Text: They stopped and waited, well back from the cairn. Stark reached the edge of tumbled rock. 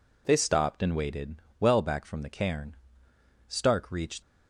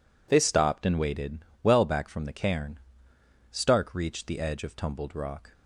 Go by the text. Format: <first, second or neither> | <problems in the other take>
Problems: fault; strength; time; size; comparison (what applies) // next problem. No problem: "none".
second | stops before "the edge of tumbled rock"; at 4.2 s